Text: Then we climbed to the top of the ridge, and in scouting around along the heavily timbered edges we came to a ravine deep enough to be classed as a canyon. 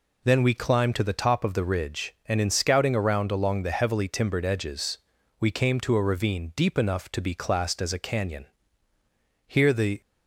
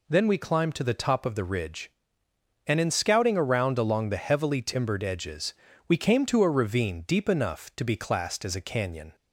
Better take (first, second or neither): second